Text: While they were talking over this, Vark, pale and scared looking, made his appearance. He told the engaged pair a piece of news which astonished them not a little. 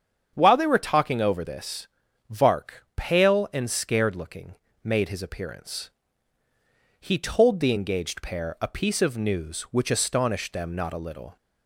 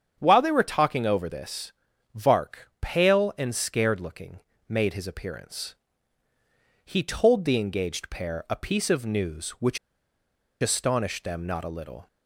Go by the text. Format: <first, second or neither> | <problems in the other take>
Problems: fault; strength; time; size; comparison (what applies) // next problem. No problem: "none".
first | starts louder than the rest; strong; until 1.2 s; 7.5 dB; strong in the first // pauses between "which" and "astonished"; noticeable; at 9.7 s; 0.82 s long